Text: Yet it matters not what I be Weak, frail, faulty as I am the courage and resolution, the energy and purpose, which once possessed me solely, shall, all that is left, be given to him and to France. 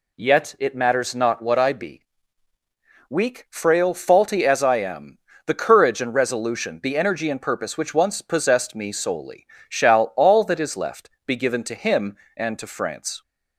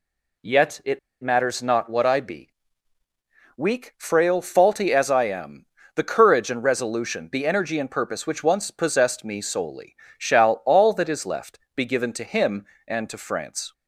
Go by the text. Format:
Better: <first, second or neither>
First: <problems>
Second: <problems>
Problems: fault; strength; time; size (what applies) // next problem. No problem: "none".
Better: first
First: pauses between "be" and "Weak"; at 2.0 s; 1.0 s long // pauses between "am" and "the"; slight; at 5.1 s; 0.30 s long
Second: pauses between "it" and "matters"; slight; at 0.9 s; 0.23 s long // pauses between "be" and "Weak"; at 2.4 s; 1.0 s long // pauses between "am" and "the"; slight; at 5.6 s; 0.32 s long